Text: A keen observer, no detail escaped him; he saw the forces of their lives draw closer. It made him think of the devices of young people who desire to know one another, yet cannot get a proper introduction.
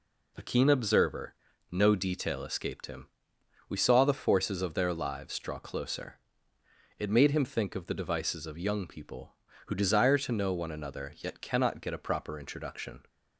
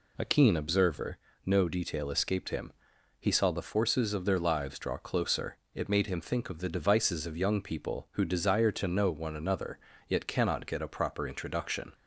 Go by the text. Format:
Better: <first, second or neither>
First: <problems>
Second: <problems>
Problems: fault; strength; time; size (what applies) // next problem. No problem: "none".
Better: second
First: says "we" for "he"; at 3.6 s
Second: none